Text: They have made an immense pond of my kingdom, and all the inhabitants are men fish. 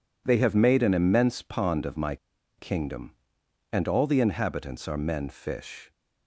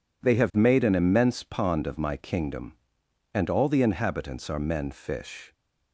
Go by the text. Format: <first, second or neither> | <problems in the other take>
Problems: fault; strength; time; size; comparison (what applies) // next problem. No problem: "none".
second | pauses between "my" and "kingdom"; at 2.1 s; 0.42 s long